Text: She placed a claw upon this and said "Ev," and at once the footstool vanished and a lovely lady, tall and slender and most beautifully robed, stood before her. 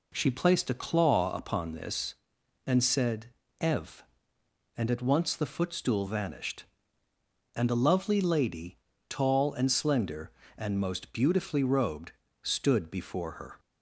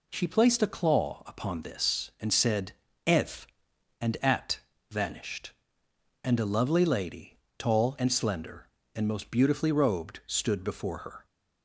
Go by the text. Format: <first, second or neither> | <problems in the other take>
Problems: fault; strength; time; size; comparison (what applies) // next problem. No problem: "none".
first | pauses between "said" and "Ev"; slight; at 2.7 s; 0.34 s long; slight in the first // skips "once the footstool"; at 4.7 s